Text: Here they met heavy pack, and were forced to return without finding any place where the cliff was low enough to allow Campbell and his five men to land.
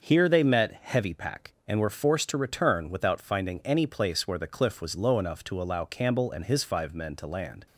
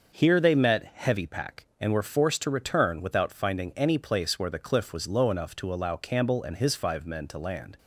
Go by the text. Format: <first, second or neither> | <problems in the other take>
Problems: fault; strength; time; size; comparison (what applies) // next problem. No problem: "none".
neither | starts louder than the rest; the same in both